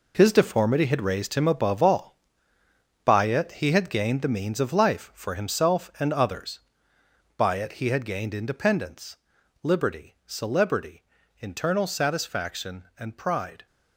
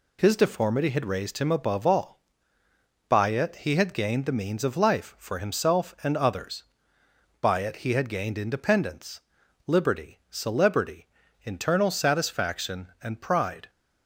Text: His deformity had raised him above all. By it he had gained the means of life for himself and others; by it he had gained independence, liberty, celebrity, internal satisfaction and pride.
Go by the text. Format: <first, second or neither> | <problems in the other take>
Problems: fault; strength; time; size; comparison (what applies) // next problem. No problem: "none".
second | gets quieter; strong; throughout; 10 dB